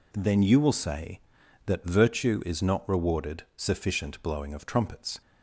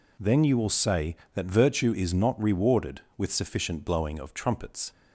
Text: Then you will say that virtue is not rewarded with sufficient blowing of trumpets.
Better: second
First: skips "with"; at 3.5 s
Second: none

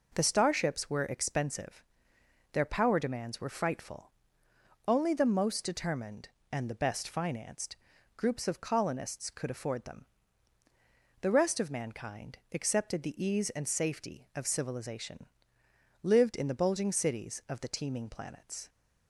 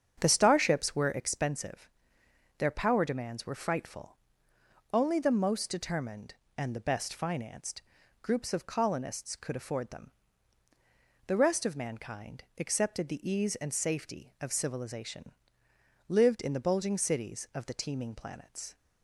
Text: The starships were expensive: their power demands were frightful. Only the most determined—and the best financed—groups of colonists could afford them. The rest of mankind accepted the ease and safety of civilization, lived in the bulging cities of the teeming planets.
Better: first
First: pauses between "mankind" and "accepted"; slight; at 12.3 s; 0.16 s long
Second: starts louder than the rest; strong; until 1.3 s; 7.5 dB // pauses between "mankind" and "accepted"; slight; at 12.4 s; 0.16 s long

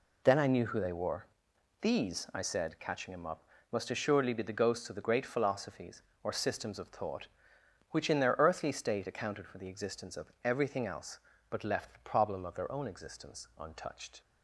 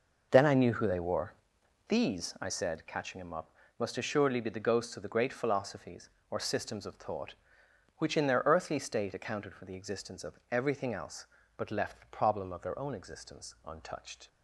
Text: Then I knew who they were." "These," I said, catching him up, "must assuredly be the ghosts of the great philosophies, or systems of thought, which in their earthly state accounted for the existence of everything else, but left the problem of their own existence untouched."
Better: first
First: none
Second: starts louder than the rest; noticeable; until 2.1 s; 5.5 dB

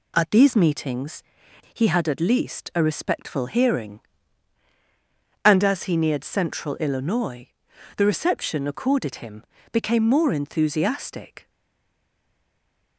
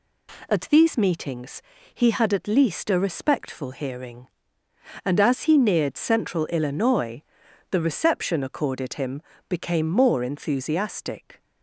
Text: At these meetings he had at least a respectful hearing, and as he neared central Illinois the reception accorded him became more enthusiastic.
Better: second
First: pauses between "meetings" and "he"; noticeable; at 1.2 s; 0.50 s long // pauses between "Illinois" and "the"; noticeable; at 7.4 s; 0.48 s long // pauses between "him" and "became"; slight; at 9.4 s; 0.30 s long // stays silent after the last word; noticeable; from 11.4 s on; 1.5 s long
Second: pauses between "meetings" and "he"; slight; at 1.6 s; 0.32 s long // pauses between "Illinois" and "the"; noticeable; at 7.2 s; 0.48 s long // pauses between "him" and "became"; slight; at 9.2 s; 0.26 s long

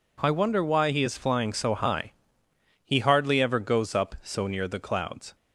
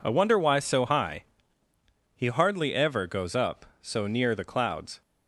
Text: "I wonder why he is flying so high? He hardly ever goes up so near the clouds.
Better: first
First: none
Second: skips "he is flying"; at 0.5 s

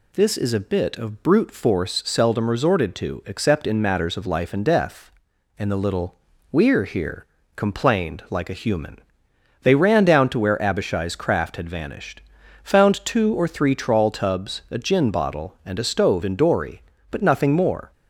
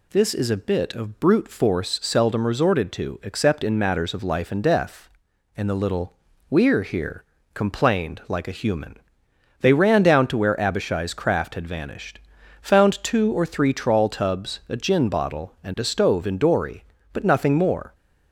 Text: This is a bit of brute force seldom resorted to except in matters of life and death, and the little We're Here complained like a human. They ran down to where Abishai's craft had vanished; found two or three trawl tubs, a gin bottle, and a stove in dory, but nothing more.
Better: neither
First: pauses between "little" and "We're"; slight; at 6.1 s; 0.34 s long // pauses between "Here" and "complained"; slight; at 7.2 s; 0.28 s long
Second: pauses between "little" and "We're"; slight; at 6.1 s; 0.34 s long // pauses between "Here" and "complained"; slight; at 7.2 s; 0.28 s long

